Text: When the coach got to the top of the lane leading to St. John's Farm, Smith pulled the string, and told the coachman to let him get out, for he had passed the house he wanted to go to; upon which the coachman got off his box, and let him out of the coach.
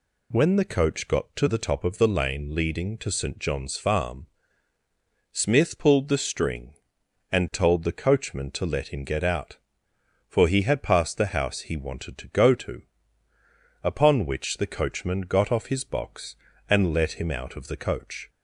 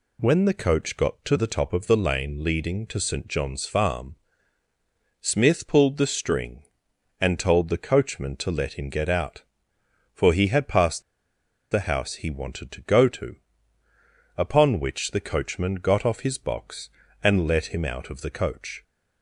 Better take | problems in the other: first | pauses between "passed" and "the"; noticeable; at 11.0 s; 0.68 s long

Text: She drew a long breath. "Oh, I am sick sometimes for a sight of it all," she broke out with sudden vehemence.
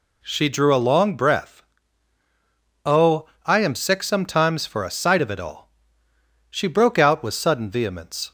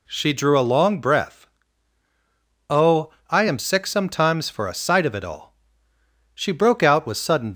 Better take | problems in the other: first | stops before "vehemence"; at 7.5 s

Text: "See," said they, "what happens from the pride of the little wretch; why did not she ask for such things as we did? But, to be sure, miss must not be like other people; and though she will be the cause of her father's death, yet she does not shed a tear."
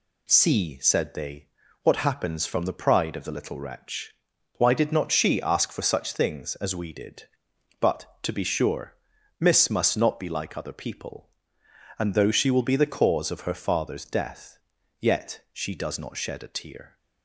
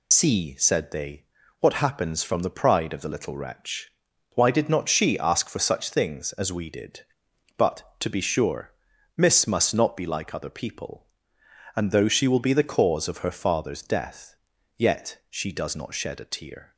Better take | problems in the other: first | loses the start of "See"; at 0.1 s; 50 ms

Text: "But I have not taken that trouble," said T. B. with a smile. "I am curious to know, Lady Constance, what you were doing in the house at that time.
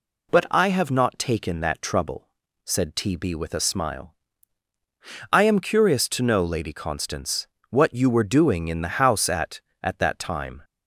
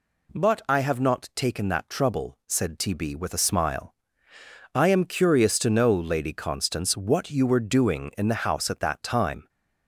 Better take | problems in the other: second | says "at" twice; at 9.8 s

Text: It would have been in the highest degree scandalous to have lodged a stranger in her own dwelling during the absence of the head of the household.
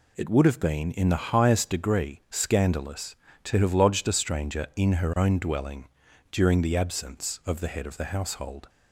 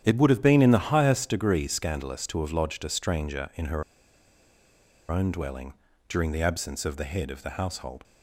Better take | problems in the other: first | starts louder than the rest; strong; until 1.0 s; 9.5 dB // pauses between "her" and "own"; strong; at 3.8 s; 1.2 s long // pauses between "dwelling" and "during"; slight; at 5.7 s; 0.34 s long; also in the first

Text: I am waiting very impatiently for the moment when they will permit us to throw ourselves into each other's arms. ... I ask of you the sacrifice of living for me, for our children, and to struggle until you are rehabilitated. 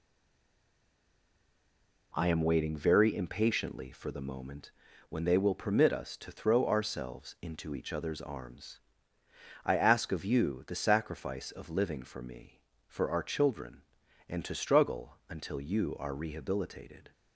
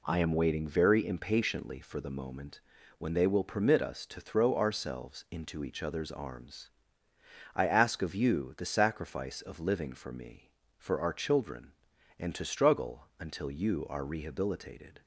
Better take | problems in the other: second | stays silent before the first word; until 2.1 s; 2.1 s long // pauses between "moment" and "when"; at 4.7 s; 0.38 s long; also in the second

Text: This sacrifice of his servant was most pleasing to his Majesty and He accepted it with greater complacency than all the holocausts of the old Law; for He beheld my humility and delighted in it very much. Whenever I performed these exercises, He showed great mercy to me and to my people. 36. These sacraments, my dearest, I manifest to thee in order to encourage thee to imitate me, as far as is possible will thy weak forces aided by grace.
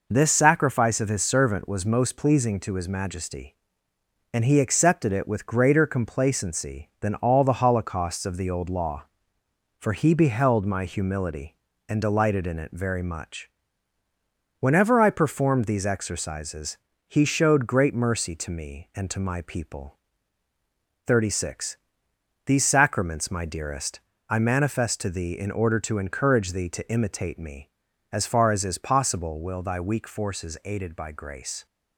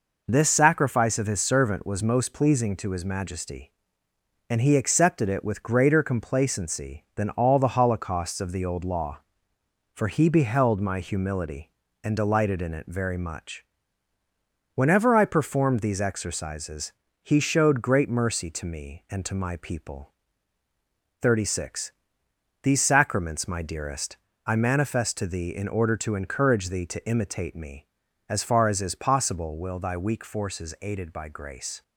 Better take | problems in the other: neither | none

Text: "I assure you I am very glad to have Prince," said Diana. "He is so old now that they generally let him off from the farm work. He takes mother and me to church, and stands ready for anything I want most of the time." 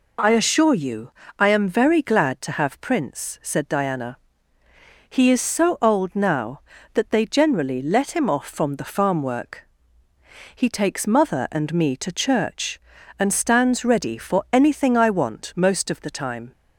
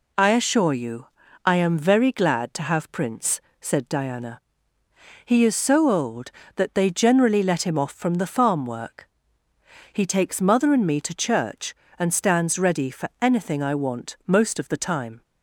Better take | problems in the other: first | pauses between "you" and "I"; at 1.0 s; 0.38 s long; slight in the first // skips "now"; at 6.4 s

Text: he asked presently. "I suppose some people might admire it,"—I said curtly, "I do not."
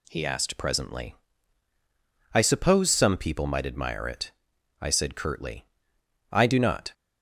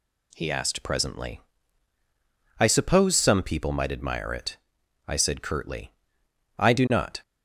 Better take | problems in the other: neither | none

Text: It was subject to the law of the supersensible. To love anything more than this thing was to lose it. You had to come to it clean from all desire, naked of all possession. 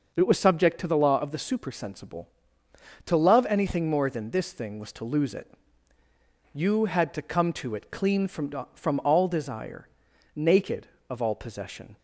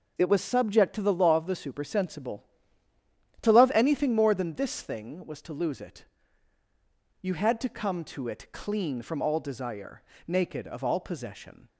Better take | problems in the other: second | says "from" twice; at 8.7 s

